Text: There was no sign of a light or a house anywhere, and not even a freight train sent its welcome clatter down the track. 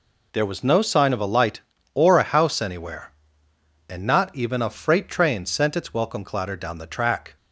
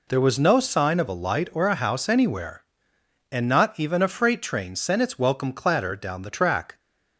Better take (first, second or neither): neither